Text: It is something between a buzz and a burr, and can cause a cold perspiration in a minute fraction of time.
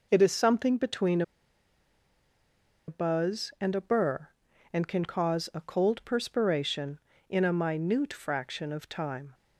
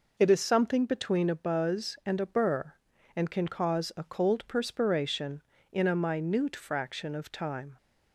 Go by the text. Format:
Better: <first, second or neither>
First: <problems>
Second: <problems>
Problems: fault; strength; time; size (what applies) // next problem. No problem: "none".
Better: second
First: pauses between "between" and "a"; strong; at 1.2 s; 1.6 s long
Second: none